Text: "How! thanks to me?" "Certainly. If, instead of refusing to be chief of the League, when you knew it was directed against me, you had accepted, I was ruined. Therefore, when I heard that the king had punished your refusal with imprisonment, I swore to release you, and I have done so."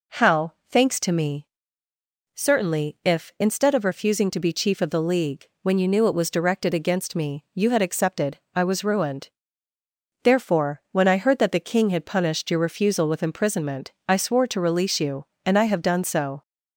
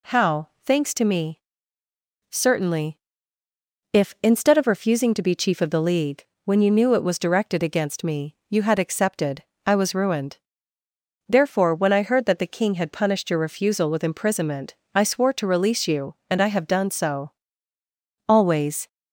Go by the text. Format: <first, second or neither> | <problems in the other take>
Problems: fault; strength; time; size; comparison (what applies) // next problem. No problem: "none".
first | goes on to say "Always"; from 18.2 s on; 0.60 s long